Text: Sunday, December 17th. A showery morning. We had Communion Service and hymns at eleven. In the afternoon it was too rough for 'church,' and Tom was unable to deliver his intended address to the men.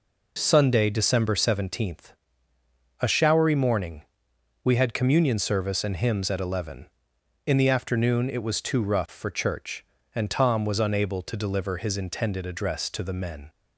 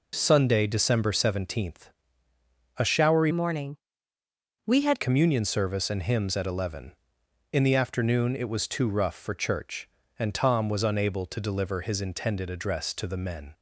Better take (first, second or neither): first